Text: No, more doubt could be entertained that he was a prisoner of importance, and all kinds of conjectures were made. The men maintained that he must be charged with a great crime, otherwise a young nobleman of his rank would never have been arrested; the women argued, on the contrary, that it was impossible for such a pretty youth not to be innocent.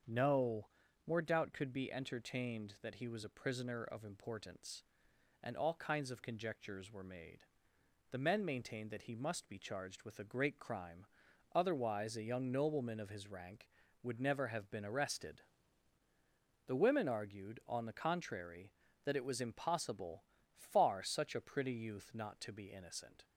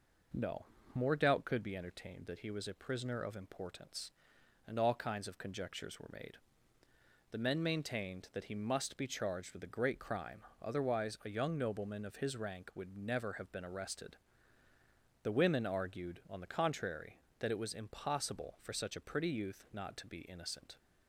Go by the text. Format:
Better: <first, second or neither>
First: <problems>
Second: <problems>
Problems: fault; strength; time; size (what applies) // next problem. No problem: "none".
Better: second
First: starts louder than the rest; until 1.4 s; 7 dB // says "far" for "for"; at 20.5 s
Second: none